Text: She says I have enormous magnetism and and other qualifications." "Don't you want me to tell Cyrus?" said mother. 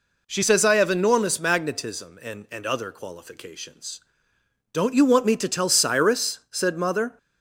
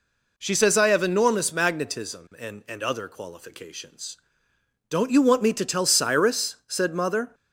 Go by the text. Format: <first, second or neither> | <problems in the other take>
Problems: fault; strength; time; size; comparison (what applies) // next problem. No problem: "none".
neither | none